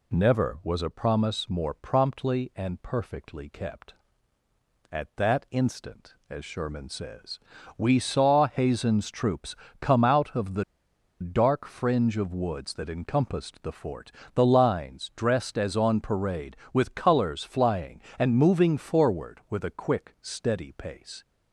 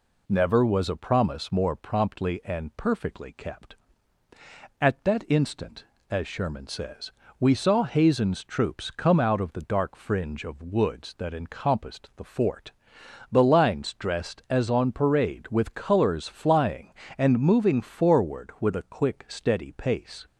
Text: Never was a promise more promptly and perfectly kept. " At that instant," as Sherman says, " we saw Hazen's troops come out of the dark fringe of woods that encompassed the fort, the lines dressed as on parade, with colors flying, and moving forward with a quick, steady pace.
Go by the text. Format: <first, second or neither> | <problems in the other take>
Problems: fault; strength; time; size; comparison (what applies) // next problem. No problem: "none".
second | pauses between "troops" and "come"; slight; at 9.5 s; 0.24 s long // pauses between "the" and "dark"; noticeable; at 10.6 s; 0.58 s long